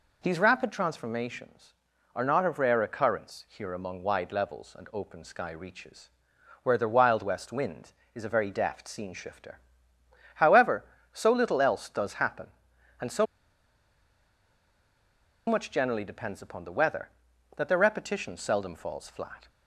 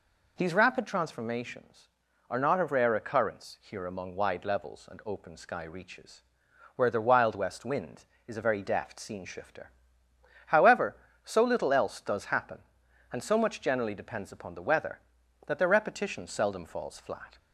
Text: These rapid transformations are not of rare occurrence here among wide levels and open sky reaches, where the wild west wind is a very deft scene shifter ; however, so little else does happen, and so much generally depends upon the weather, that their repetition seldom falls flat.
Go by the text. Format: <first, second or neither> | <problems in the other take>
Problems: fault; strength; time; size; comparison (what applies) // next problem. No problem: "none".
second | pauses between "so" and "much"; strong; at 13.2 s; 2.2 s long